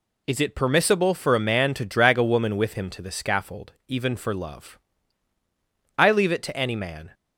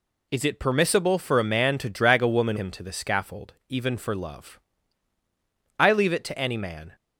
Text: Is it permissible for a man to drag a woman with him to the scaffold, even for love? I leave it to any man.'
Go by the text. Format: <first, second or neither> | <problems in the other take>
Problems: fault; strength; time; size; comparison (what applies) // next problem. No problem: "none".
first | skips "with"; at 2.5 s